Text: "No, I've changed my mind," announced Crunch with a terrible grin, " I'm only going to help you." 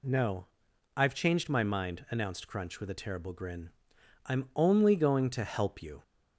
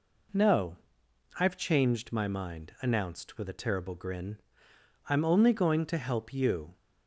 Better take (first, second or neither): first